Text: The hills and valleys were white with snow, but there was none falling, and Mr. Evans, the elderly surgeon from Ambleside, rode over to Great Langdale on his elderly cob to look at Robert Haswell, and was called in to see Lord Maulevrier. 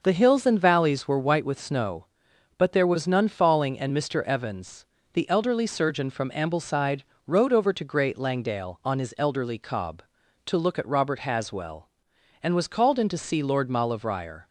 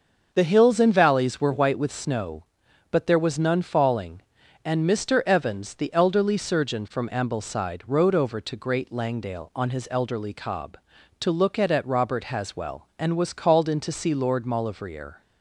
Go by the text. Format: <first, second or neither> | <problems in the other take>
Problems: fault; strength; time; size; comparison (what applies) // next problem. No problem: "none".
first | starts louder than the rest; until 1.3 s; 6.5 dB; noticeable in the first // says "at" twice; at 11.6 s